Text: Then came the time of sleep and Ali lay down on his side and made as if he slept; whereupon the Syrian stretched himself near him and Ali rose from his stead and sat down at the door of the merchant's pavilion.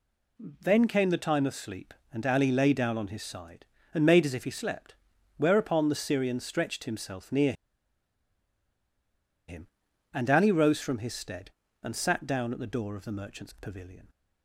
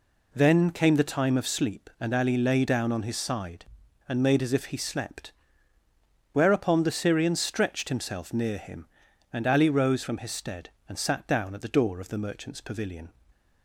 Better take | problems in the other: second | pauses between "near" and "him"; strong; at 7.5 s; 1.9 s long

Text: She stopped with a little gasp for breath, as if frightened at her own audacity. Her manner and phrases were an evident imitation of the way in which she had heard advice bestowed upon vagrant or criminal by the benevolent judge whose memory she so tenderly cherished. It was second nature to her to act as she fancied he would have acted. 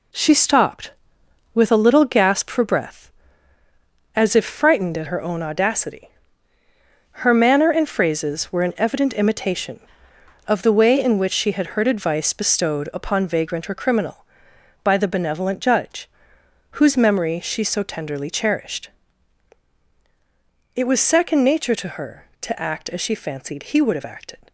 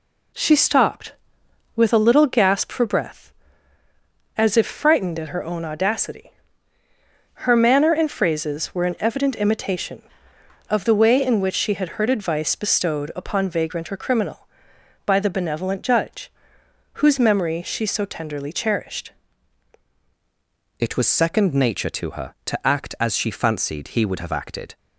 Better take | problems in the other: first | pauses between "judge" and "whose"; noticeable; at 16.3 s; 0.66 s long; noticeable in the first // changes voice at "It"; from 20.7 s on; 4.0 s long

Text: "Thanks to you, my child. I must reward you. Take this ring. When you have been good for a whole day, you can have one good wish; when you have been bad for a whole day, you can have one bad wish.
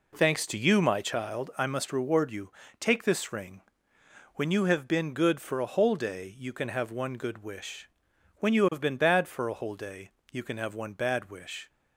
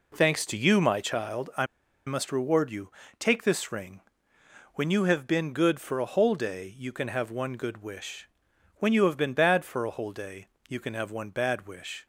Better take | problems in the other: first | pauses between "I" and "must"; at 1.6 s; 0.41 s long

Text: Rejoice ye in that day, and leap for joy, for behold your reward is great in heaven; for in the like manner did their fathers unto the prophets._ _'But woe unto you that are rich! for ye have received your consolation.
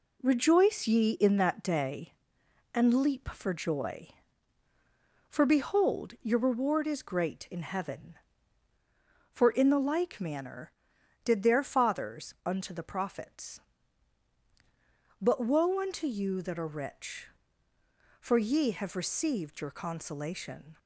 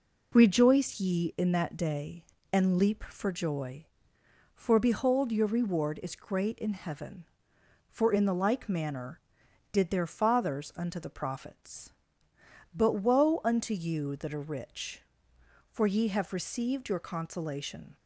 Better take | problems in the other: neither | none

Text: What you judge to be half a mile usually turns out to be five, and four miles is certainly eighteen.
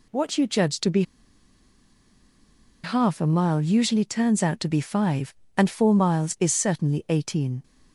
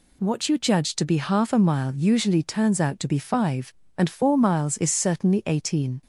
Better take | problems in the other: second | pauses between "be" and "half"; strong; at 1.0 s; 1.8 s long

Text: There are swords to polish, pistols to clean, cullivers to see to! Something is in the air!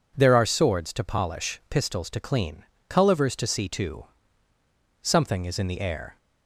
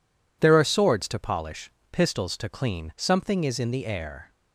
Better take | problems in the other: first | skips "cullivers to see to"; at 2.9 s

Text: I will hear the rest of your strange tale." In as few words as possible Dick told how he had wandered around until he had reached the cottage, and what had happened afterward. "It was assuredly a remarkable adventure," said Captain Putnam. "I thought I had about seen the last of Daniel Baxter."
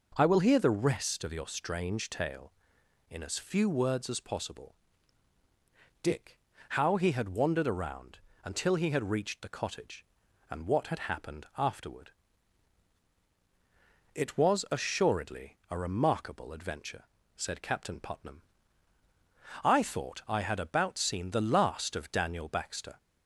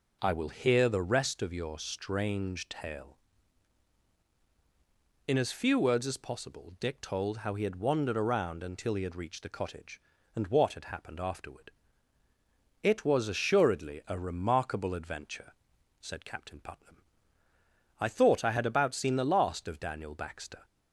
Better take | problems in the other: second | pauses between "possible" and "Dick"; strong; at 4.7 s; 1.2 s long // skips "told"; at 6.5 s // pauses between "around" and "until"; slight; at 8.1 s; 0.26 s long

